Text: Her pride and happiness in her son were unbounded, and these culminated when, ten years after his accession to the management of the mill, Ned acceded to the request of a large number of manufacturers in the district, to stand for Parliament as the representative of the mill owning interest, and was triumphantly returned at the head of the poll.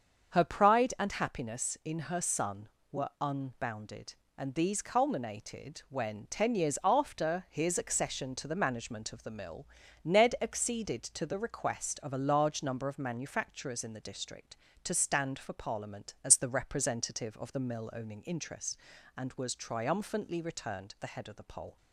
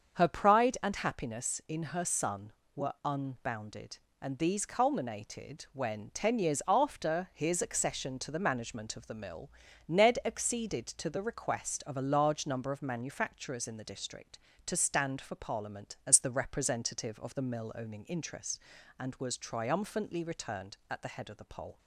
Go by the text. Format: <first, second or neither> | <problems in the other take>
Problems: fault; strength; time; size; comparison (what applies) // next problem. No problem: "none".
second | starts louder than the rest; until 1.4 s; 7 dB; also in the second // skips "at"; at 20.9 s